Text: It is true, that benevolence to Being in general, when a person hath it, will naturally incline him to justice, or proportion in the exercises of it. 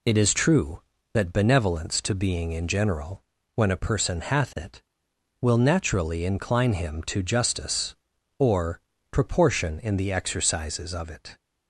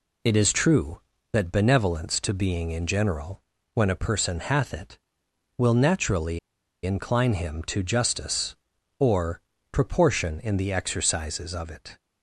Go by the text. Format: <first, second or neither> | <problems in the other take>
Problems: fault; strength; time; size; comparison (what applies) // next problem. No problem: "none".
first | pauses between "naturally" and "incline"; noticeable; at 6.3 s; 0.46 s long // pauses between "or" and "proportion"; slight; at 9.4 s; 0.28 s long; slight in the first